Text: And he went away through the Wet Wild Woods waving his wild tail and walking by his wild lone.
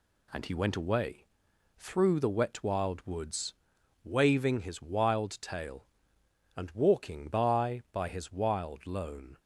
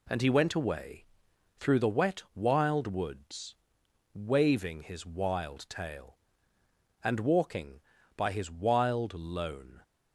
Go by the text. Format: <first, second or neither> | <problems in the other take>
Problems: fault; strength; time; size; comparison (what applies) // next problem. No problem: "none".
second | pauses between "away" and "through"; noticeable; at 1.2 s; 0.52 s long; noticeable in the second // pauses between "Woods" and "waving"; noticeable; at 3.5 s; 0.50 s long; noticeable in the second // says "by" twice; at 7.9 s